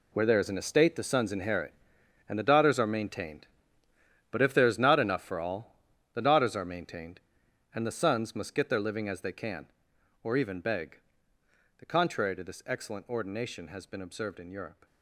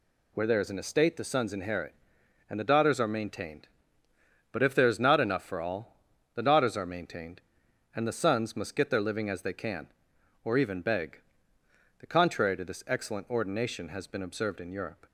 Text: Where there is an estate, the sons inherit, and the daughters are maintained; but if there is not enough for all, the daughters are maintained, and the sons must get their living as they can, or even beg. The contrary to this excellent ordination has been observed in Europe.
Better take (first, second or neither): second